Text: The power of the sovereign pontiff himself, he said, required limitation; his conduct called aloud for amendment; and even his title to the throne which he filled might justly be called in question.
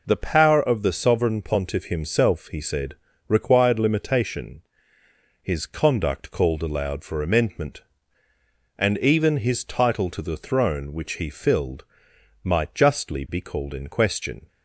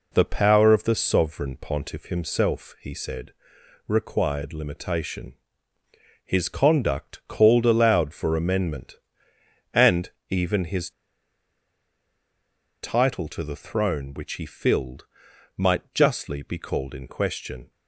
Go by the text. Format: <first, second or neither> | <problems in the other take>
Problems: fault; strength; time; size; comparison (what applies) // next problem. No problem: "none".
first | pauses between "and" and "even"; slight; at 10.1 s; 0.18 s long // pauses between "his" and "title"; strong; at 10.9 s; 1.9 s long // pauses between "filled" and "might"; noticeable; at 15.0 s; 0.50 s long; noticeable in the first